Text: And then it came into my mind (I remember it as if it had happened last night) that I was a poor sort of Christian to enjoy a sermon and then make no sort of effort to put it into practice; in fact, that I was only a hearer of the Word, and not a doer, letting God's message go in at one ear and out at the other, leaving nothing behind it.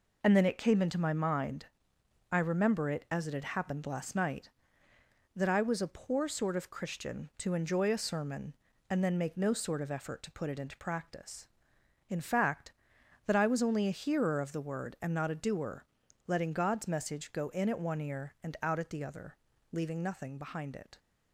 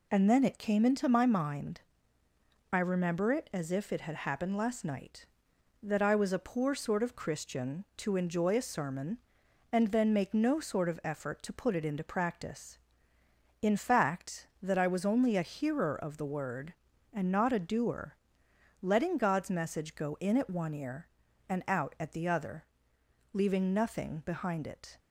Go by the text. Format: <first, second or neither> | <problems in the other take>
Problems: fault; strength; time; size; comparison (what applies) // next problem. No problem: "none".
second | skips "if"; at 3.2 s